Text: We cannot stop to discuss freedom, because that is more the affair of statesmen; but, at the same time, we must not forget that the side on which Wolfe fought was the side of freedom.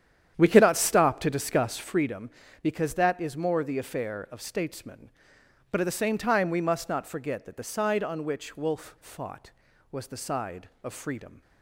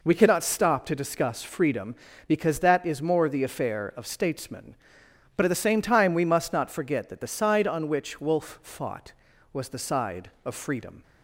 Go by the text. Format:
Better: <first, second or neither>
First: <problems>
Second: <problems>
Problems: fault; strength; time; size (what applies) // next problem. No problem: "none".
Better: second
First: starts louder than the rest; strong; until 2.1 s; 9.5 dB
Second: none